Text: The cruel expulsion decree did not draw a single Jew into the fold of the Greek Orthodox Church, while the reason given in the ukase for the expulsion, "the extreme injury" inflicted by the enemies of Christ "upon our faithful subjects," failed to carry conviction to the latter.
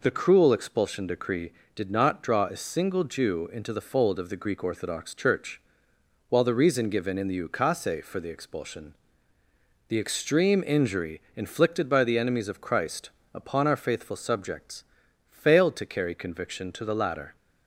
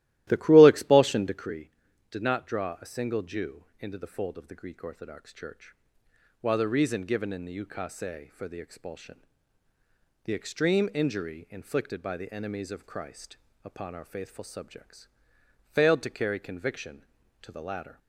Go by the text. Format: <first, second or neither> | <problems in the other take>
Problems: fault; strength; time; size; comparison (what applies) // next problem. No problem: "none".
first | starts louder than the rest; strong; until 1.6 s; 15.5 dB // pauses between "Jew" and "into"; slight; at 3.6 s; 0.16 s long // pauses between "Christ" and "upon"; slight; at 13.3 s; 0.26 s long; slight in the first